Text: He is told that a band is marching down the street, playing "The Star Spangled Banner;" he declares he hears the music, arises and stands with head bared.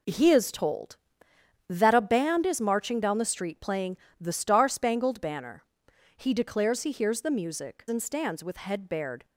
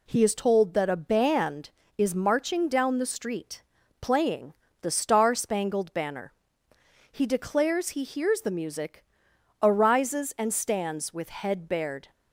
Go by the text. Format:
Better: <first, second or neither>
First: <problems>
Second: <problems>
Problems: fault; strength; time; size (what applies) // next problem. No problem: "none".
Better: second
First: pauses between "playing" and "The"; slight; at 3.9 s; 0.24 s long // skips "arises"; at 7.8 s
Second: pauses between "playing" and "The"; slight; at 4.5 s; 0.28 s long